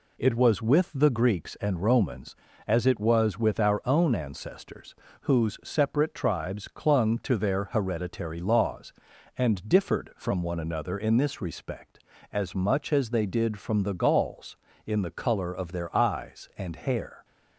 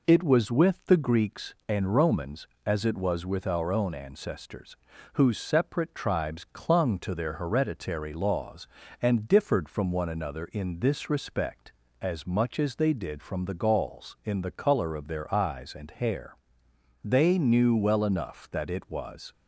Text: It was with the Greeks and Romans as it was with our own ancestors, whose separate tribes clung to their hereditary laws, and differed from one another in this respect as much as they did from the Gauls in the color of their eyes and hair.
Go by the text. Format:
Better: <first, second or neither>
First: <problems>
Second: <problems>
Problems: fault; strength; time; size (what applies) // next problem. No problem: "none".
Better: first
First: none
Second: goes on to say "They knew well enough that it was"; strong; from 17.0 s on; 2.2 s long